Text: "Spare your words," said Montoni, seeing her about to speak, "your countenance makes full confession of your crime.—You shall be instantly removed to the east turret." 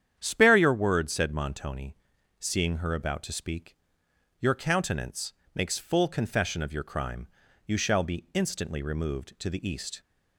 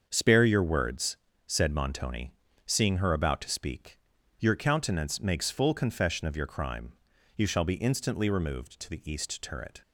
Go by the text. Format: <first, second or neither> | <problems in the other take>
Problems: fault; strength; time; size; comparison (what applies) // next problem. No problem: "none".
second | starts louder than the rest; strong; until 1.2 s; 9 dB; also in the second // pauses between "countenance" and "makes"; slight; at 5.3 s; 0.20 s long // stops before "turret"; at 9.9 s